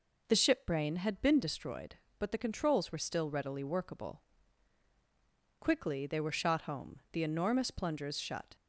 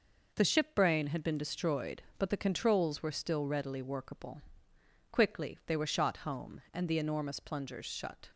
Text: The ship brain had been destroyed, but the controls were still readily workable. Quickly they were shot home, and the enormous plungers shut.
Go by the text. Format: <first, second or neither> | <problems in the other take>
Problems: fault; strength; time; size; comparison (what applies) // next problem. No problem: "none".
second | skips "and"; at 7.0 s